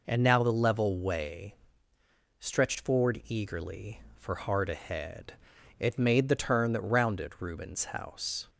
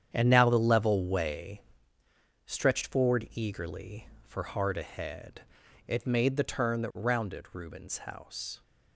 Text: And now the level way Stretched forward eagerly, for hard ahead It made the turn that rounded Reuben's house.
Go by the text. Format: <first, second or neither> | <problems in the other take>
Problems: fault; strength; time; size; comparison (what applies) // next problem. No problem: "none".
first | gets quieter; strong; throughout; 11.5 dB // pauses between "way" and "Stretched"; noticeable; at 1.6 s; 0.88 s long; noticeable in the first // pauses between "ahead" and "It"; at 5.4 s; 0.44 s long; also in the first